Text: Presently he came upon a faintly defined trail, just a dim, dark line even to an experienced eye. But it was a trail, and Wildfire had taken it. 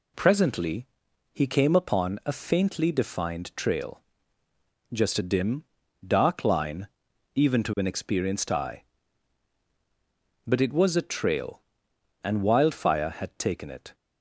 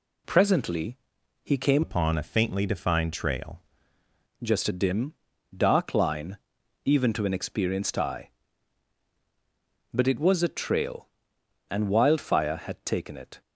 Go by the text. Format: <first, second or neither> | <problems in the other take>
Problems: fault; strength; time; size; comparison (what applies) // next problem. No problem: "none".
first | pauses between "Presently" and "he"; noticeable; at 0.9 s; 0.46 s long; noticeable in the first // changes voice from "upon" to "trail"; from 1.8 to 3.6 s; 1.8 s long // pauses between "line" and "even"; noticeable; at 6.3 s; 0.48 s long; noticeable in the first